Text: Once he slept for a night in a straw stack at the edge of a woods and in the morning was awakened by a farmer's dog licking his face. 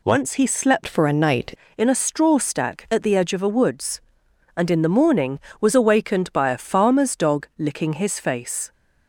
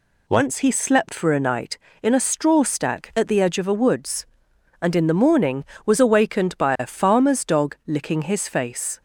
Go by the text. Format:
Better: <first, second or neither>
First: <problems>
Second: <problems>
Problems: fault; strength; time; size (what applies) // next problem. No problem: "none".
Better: second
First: changes voice from "for" to "night"; from 0.8 to 1.5 s; 0.7 s long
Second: none